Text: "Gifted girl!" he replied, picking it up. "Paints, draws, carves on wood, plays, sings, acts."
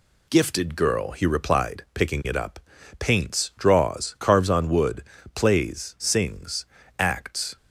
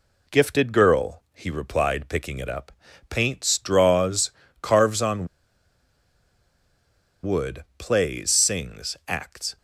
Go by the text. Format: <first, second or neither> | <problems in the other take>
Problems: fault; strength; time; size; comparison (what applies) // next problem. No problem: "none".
first | pauses between "on" and "wood"; strong; at 5.2 s; 1.9 s long